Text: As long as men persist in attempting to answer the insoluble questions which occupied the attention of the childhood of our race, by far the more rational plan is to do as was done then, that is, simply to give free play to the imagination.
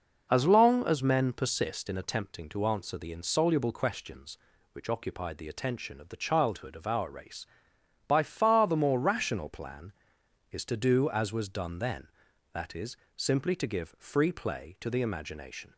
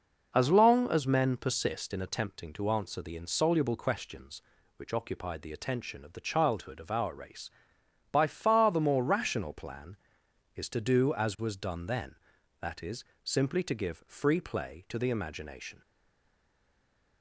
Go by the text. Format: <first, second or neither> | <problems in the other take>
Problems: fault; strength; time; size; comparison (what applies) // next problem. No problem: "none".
first | stays silent after the last word; noticeable; from 15.8 s on; 1.4 s long